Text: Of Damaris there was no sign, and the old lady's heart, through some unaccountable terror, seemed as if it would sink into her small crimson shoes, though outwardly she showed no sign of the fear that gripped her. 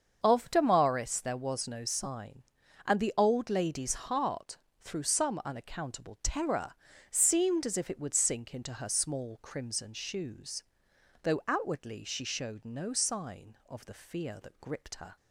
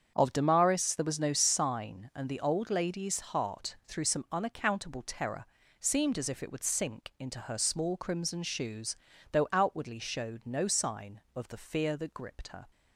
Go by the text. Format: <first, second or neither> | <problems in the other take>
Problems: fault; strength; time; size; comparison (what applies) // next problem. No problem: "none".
first | starts louder than the rest; strong; until 1.1 s; 7.5 dB; also in the first // skips "she"; at 9.9 s